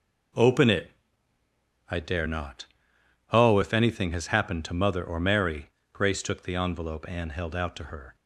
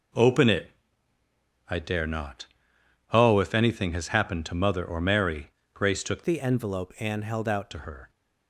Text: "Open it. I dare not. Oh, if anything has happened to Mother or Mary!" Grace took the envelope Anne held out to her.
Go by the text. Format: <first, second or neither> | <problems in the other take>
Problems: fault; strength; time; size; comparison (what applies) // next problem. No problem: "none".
first | changes voice from "the" to "out"; from 6.2 to 7.7 s; 1.5 s long